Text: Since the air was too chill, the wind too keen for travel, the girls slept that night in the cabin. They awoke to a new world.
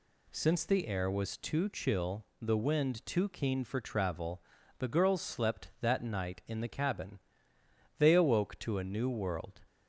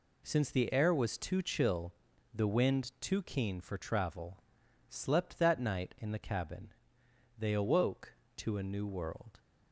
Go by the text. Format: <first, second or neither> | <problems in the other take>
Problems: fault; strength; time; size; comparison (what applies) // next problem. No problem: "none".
first | skips "the girls"; at 4.6 s